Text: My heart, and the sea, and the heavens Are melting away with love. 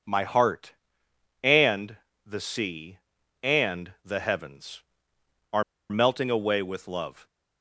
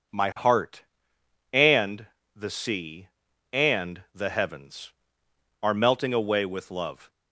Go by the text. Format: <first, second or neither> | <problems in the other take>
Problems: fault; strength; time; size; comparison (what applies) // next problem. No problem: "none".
second | pauses between "and" and "the"; slight; at 1.9 s; 0.32 s long; slight in the second // pauses between "Are" and "melting"; slight; at 5.6 s; 0.26 s long